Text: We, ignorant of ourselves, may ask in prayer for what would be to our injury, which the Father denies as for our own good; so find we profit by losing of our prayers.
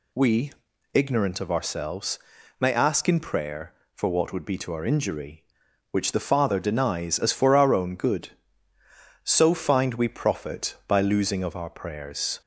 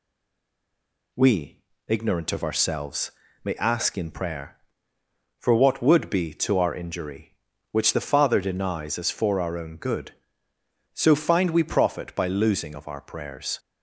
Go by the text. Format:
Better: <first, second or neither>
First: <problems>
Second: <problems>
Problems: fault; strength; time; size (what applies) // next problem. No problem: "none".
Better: first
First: none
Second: stays silent before the first word; until 1.1 s; 1.1 s long